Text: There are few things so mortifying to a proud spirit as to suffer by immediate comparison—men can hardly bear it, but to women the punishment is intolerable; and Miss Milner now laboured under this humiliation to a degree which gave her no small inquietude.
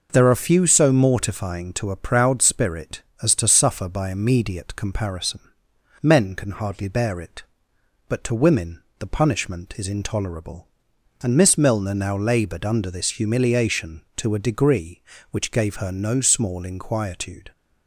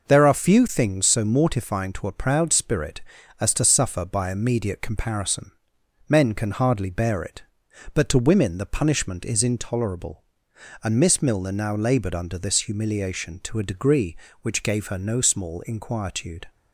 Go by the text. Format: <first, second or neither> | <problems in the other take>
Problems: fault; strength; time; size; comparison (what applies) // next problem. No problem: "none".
second | skips "things"; at 0.6 s // pauses between "women" and "the"; slight; at 8.8 s; 0.16 s long